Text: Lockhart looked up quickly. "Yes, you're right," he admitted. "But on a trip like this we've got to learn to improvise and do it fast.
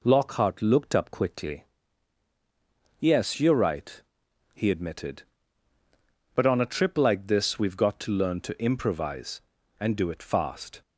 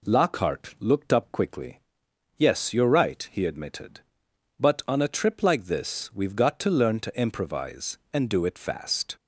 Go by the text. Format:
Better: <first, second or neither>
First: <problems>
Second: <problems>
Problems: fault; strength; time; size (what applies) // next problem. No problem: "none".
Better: neither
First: none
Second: none